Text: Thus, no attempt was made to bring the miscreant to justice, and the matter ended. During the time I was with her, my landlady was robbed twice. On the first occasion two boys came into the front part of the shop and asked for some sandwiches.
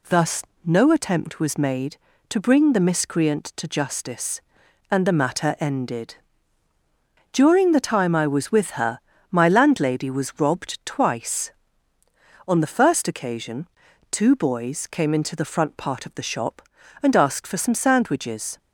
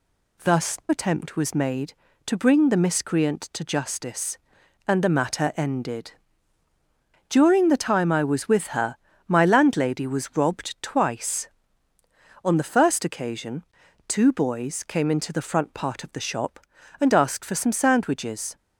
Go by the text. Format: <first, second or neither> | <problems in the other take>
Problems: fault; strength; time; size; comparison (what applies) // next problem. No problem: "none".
first | skips "no"; at 0.8 s // pauses between "occasion" and "two"; at 13.6 s; 0.44 s long; also in the first